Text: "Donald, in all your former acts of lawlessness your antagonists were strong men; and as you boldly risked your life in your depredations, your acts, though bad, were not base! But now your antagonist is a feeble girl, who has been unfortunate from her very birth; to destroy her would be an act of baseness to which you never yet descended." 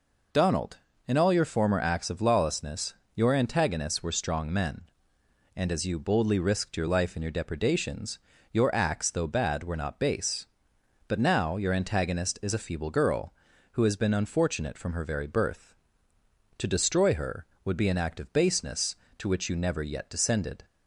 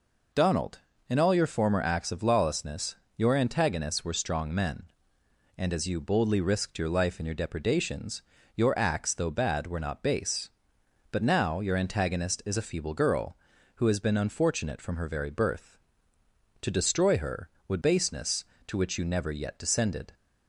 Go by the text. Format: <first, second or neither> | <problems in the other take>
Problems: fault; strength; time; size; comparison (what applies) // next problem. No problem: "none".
first | pauses between "lawlessness" and "your"; slight; at 2.9 s; 0.20 s long; slight in the first // skips "be an act of"; at 17.8 s